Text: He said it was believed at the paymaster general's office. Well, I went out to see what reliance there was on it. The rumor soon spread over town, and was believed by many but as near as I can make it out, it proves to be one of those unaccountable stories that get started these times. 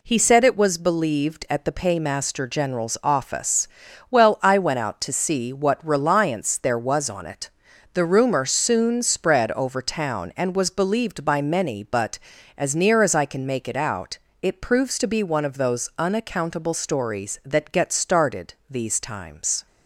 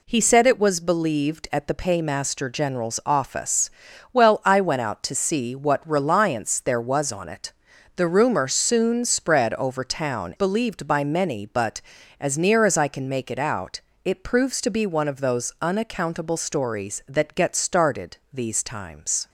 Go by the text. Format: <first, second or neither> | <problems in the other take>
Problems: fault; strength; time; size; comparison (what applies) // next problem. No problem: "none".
first | skips "and was"; at 10.3 s // pauses between "started" and "these"; slight; at 18.1 s; 0.16 s long; slight in the first